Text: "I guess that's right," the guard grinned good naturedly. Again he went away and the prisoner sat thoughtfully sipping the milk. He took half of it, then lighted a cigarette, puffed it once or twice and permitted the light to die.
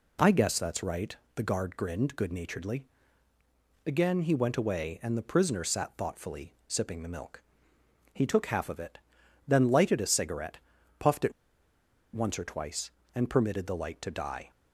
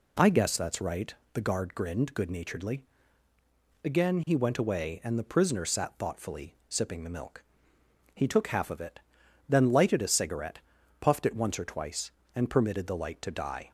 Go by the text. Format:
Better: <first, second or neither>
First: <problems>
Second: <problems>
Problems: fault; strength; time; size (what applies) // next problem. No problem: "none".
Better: second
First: pauses between "it" and "once"; noticeable; at 11.3 s; 0.82 s long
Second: none